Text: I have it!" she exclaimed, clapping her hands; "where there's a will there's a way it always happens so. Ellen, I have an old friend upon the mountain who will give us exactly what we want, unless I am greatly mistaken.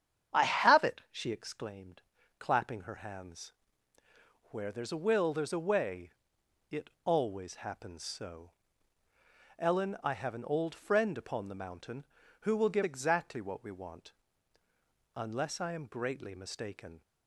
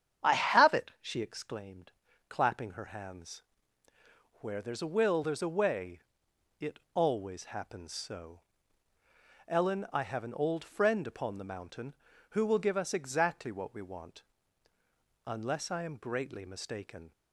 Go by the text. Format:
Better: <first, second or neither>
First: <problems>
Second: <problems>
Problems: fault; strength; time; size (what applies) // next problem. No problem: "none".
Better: second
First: starts louder than the rest; strong; until 1.4 s; 8.5 dB // pauses between "way" and "it"; noticeable; at 6.1 s; 0.60 s long // pauses between "it" and "always"; slight; at 6.9 s; 0.16 s long // skips "us"; at 12.8 s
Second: starts louder than the rest; strong; until 1.3 s; 8.5 dB // pauses between "way" and "it"; noticeable; at 5.9 s; 0.60 s long // pauses between "it" and "always"; slight; at 6.7 s; 0.16 s long